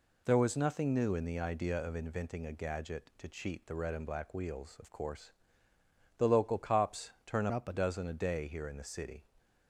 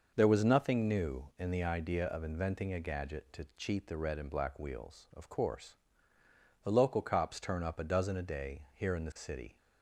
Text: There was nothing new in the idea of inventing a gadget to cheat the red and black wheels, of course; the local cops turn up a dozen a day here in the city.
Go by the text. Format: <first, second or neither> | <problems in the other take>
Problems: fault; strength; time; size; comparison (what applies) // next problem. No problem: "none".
second | pauses between "cops" and "turn"; slight; at 7.0 s; 0.16 s long // changes voice from "up" to "a"; from 7.5 to 7.7 s; 0.2 s long